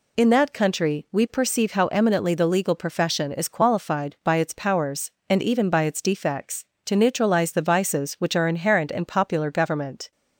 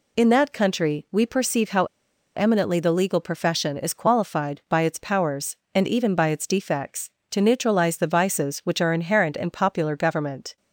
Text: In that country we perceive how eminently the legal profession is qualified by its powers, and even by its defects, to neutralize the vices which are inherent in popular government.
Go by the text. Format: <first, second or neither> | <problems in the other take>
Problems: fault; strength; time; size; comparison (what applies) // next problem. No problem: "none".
first | pauses between "how" and "eminently"; noticeable; at 1.8 s; 0.50 s long